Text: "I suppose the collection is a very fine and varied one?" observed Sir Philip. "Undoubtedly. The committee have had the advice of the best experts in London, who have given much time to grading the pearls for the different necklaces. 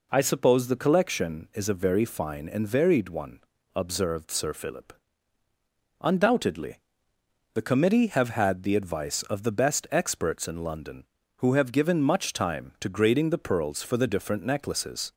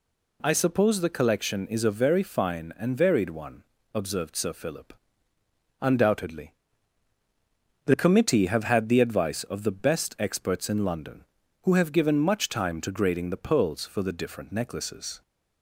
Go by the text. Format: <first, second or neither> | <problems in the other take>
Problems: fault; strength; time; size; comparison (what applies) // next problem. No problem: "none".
neither | none